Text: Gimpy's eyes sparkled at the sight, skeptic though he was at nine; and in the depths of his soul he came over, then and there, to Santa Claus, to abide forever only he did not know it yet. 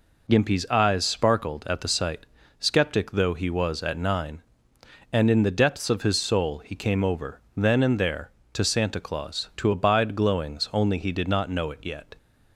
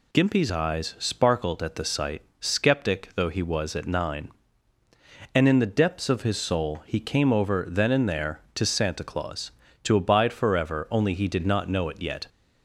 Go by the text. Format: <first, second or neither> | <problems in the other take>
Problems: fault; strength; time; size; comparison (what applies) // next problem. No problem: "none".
second | says "glowings" for "forever"; at 10.1 s